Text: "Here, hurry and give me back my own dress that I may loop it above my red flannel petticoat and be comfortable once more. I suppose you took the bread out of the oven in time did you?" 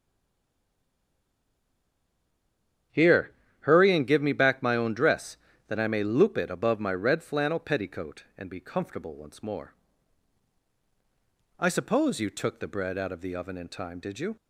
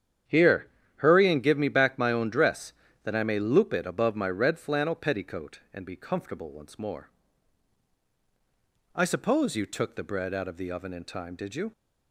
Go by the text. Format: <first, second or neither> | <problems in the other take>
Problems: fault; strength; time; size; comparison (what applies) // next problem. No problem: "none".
second | stays silent before the first word; strong; until 2.9 s; 2.9 s long // starts louder than the rest; strong; until 4.2 s; 9 dB; strong in the second